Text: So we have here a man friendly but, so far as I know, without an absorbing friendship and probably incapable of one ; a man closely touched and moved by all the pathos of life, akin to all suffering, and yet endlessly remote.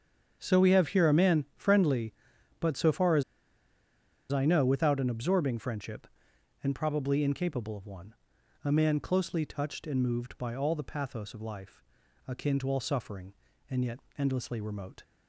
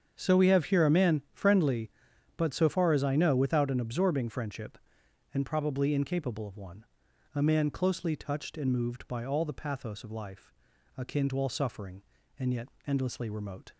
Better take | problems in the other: second | starts louder than the rest; strong; until 1.4 s; 7.5 dB; strong in the second // pauses between "as" and "I"; at 3.2 s; 1.0 s long // pauses between "yet" and "endlessly"; slight; at 14.0 s; 0.16 s long; slight in the second

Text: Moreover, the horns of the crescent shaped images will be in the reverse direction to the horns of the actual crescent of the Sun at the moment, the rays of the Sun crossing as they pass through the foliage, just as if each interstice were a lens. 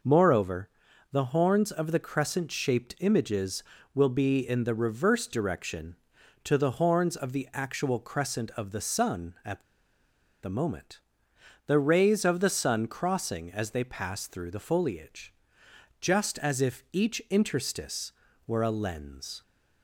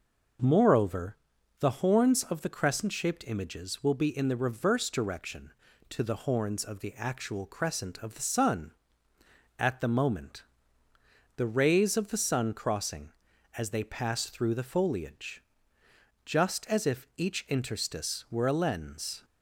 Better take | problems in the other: second | pauses between "at" and "the"; noticeable; at 9.6 s; 0.81 s long

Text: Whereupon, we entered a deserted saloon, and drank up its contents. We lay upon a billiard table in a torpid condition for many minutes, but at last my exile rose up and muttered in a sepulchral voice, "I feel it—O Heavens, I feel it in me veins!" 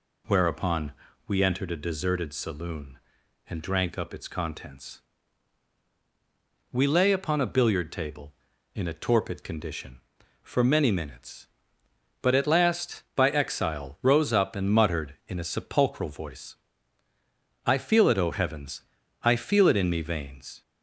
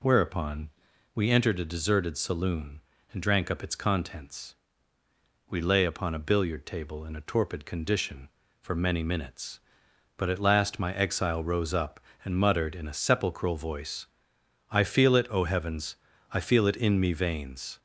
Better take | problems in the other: second | says "by" for "my"; at 13.1 s

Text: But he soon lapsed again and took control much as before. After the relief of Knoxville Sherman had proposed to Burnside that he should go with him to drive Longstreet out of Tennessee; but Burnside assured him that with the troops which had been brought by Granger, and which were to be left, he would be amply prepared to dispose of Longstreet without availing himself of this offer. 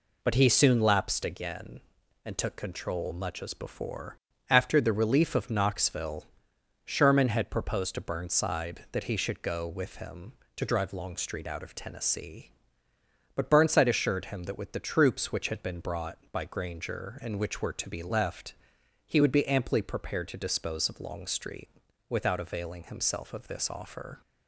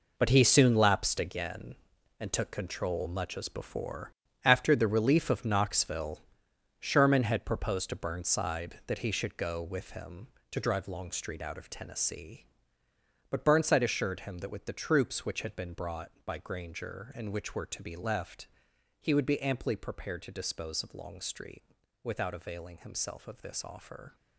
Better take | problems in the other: first | gets quieter; strong; throughout; 10.5 dB // pauses between "Knoxville" and "Sherman"; noticeable; at 6.2 s; 0.58 s long; noticeable in the first // pauses between "Longstreet" and "without"; at 21.6 s; 0.40 s long; also in the first

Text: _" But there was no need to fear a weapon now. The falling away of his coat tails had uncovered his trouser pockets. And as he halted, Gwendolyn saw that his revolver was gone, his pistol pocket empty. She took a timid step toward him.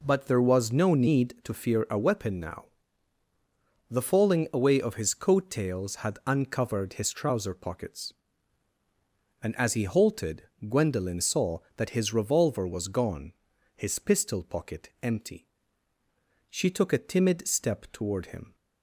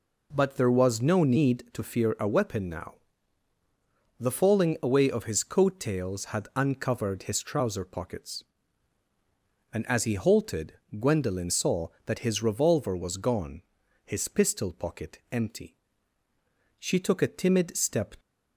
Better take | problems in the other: first | stops before "toward him"; at 18.1 s

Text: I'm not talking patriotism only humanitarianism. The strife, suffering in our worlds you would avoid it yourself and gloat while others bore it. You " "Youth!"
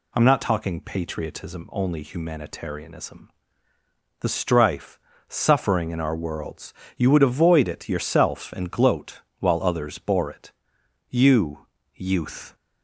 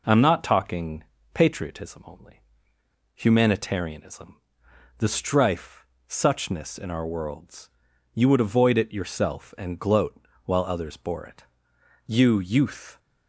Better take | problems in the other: first | pauses between "talking" and "patriotism"; slight; at 1.0 s; 0.30 s long // pauses between "only" and "humanitarianism"; noticeable; at 2.4 s; 0.73 s long // says "suchness" for "suffering"; at 6.0 s // pauses between "worlds" and "you"; at 7.7 s; 0.44 s long; slight in the first // pauses between "gloat" and "while"; slight; at 10.1 s; 0.26 s long; slight in the first

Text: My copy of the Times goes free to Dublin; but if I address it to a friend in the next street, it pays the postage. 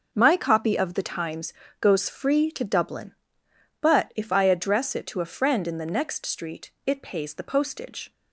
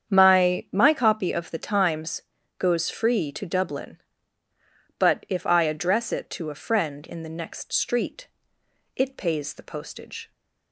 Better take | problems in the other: first | starts louder than the rest; strong; until 1.1 s; 8 dB // says "My" twice; at 0.7 s // pauses between "Times" and "goes"; at 2.2 s; 0.38 s long; slight in the first

